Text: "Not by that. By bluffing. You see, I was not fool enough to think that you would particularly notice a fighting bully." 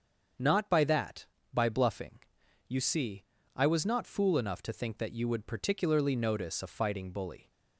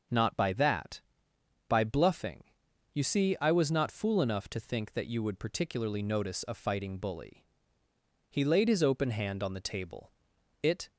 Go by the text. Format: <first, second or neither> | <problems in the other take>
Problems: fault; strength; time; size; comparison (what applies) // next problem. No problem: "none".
first | starts louder than the rest; until 1.7 s; 6.5 dB; strong in the first // goes on to say "He laid his open hand on the table It"; strong; from 8.3 s on; 2.6 s long